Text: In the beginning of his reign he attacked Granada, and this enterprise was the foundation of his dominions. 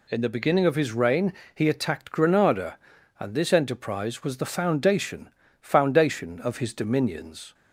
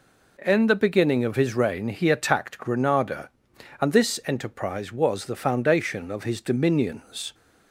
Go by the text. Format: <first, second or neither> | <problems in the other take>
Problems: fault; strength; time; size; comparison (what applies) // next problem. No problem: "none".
second | pauses between "reign" and "he"; slight; at 1.3 s; 0.20 s long // says "foundation" twice; at 5.5 s